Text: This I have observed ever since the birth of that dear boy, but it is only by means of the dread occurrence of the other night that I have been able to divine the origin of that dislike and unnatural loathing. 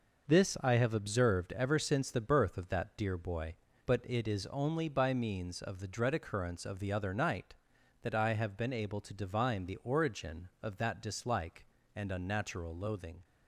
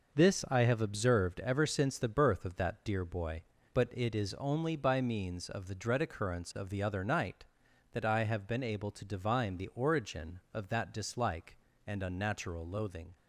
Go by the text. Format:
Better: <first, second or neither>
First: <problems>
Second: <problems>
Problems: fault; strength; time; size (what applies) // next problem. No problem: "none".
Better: neither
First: none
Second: none